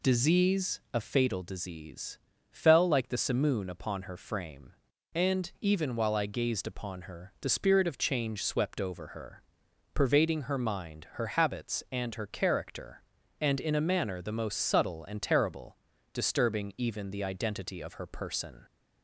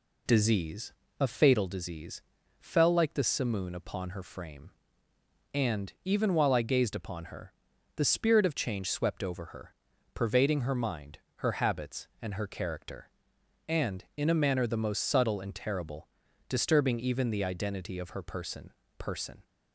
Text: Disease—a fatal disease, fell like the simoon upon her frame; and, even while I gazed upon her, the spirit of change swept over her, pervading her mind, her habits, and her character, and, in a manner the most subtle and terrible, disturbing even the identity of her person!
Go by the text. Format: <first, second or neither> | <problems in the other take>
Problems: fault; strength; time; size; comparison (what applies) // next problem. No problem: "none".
first | says "person" twice; at 18.9 s